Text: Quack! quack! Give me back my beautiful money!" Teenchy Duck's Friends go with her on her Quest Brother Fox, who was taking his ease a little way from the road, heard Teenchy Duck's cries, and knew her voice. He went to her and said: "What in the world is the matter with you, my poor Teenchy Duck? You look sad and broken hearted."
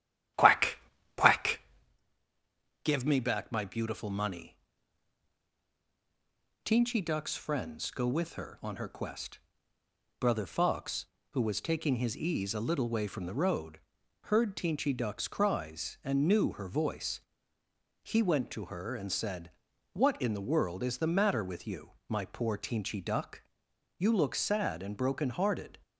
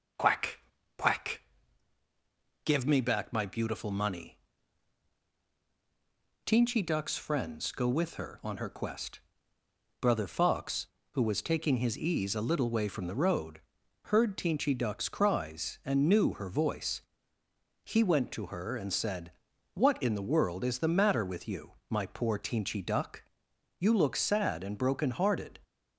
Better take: second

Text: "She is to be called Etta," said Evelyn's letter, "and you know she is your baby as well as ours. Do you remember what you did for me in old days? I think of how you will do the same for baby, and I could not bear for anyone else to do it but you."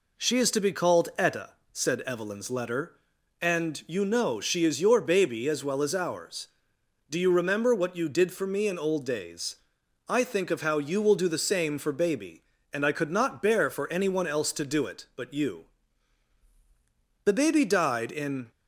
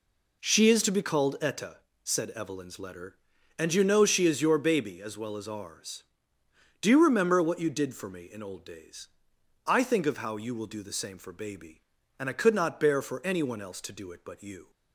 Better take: second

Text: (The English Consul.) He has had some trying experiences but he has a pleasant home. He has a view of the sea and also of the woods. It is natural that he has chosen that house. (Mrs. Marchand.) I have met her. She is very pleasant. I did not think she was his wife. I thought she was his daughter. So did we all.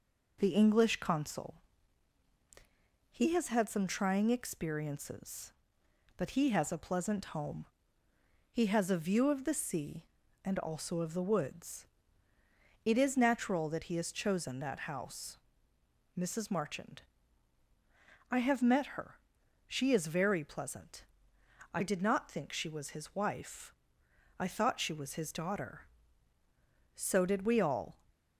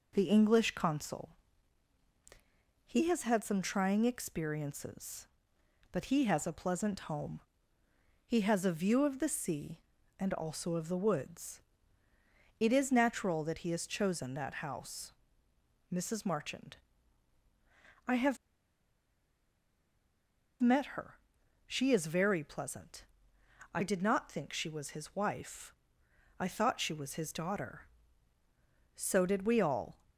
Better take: first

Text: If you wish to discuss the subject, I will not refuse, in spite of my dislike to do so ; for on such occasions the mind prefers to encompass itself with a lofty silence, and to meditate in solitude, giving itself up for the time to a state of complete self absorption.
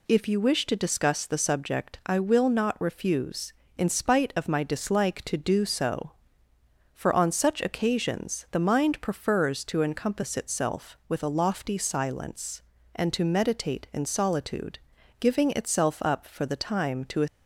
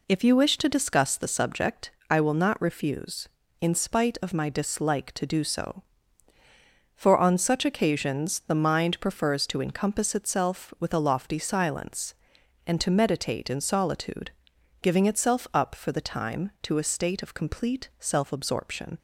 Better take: second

